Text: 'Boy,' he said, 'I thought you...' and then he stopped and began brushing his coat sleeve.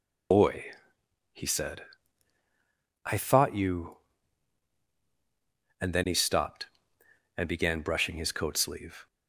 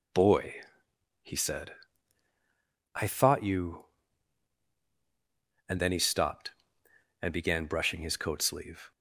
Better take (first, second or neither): second